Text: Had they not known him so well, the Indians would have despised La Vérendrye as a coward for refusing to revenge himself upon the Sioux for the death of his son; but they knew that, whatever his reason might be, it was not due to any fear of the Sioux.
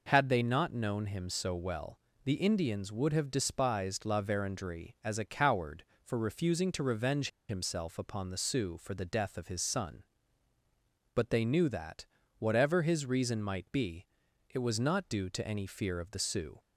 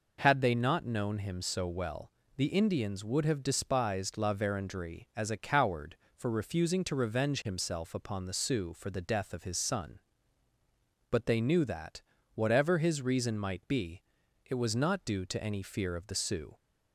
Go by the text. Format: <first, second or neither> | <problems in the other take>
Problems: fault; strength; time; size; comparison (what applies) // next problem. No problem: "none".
second | pauses between "revenge" and "himself"; slight; at 7.2 s; 0.21 s long